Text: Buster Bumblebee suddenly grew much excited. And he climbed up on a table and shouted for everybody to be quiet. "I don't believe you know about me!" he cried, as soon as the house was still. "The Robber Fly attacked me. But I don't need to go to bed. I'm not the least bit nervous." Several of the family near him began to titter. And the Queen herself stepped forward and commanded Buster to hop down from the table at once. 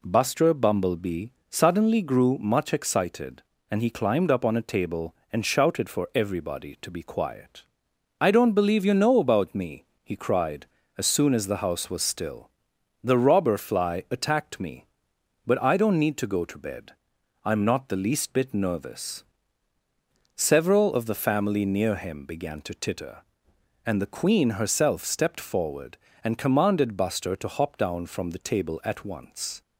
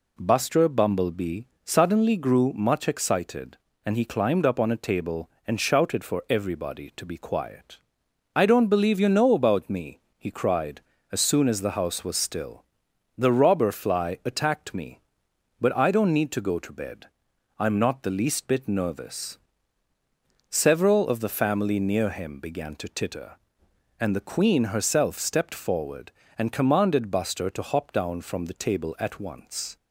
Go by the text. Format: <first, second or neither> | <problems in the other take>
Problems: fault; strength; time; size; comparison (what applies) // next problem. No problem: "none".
neither | pauses between "Bumblebee" and "suddenly"; slight; the same in both